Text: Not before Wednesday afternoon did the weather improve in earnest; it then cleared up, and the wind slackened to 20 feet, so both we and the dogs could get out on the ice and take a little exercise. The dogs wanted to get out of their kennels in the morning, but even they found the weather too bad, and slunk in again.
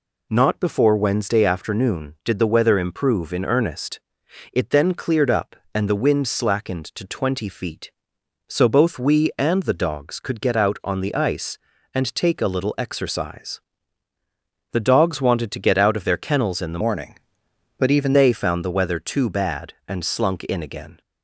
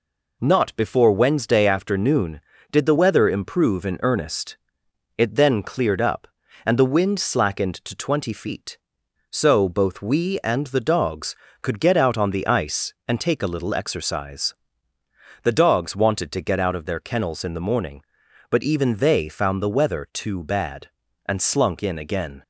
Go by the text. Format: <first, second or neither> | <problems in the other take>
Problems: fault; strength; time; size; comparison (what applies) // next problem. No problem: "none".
second | changes voice from "morning" to "even"; from 16.8 to 18.1 s; 1.3 s long